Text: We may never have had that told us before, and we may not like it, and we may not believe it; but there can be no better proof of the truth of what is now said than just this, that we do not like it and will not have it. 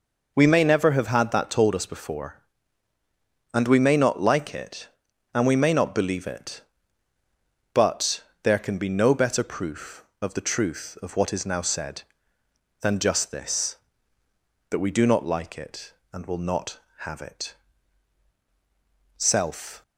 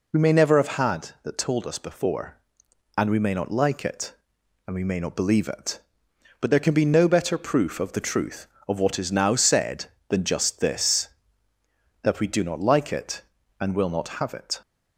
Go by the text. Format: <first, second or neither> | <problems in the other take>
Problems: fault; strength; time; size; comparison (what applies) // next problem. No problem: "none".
second | pauses between "but" and "there"; slight; at 8.2 s; 0.22 s long // goes on to say "Self"; noticeable; from 19.1 s on; 0.64 s long